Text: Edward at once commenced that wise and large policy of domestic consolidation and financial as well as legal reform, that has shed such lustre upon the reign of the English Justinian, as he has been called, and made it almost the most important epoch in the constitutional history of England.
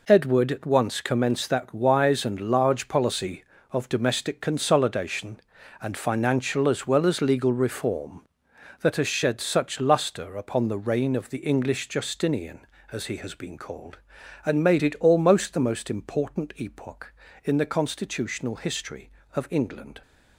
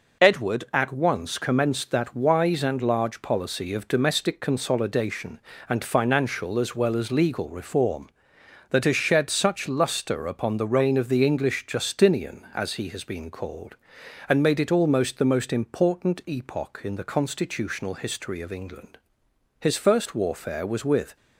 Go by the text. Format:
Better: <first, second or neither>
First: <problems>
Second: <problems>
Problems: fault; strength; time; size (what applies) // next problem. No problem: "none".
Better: first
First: none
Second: goes on to say "His first warfare was with"; from 19.5 s on; 1.5 s long